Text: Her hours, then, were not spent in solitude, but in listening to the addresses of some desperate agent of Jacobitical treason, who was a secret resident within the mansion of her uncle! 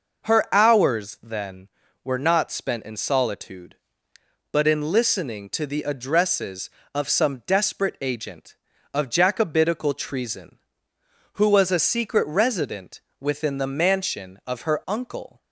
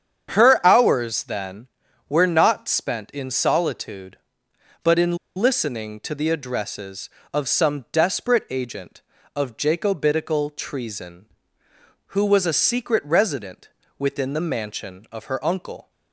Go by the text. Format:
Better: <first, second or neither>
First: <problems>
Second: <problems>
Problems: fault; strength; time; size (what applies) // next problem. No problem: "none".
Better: first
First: pauses between "resident" and "within"; slight; at 13.0 s; 0.20 s long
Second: starts louder than the rest; strong; until 1.3 s; 8 dB // pauses between "in" and "listening"; slight; at 5.1 s; 0.18 s long // pauses between "resident" and "within"; slight; at 13.6 s; 0.30 s long